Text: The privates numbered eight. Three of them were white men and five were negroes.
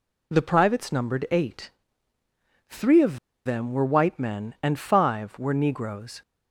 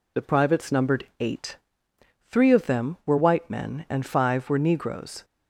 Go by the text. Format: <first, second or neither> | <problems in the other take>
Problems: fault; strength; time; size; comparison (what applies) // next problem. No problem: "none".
second | pauses between "of" and "them"; slight; at 3.1 s; 0.27 s long